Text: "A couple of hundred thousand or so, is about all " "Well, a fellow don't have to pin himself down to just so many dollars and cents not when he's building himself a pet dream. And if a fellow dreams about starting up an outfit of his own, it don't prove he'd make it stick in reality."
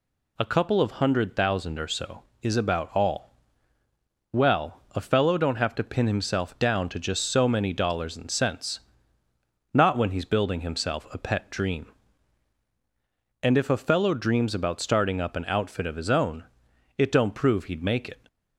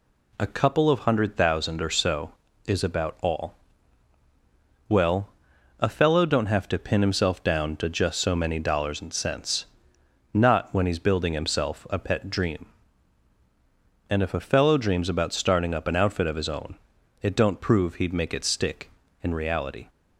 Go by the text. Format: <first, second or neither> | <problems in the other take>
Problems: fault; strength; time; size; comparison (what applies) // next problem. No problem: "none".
second | pauses between "cents" and "not"; noticeable; at 8.7 s; 0.92 s long; noticeable in the second // stops before "stick in reality"; at 18.2 s